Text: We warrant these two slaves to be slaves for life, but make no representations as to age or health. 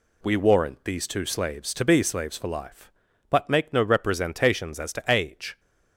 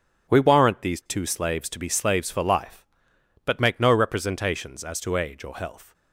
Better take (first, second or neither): second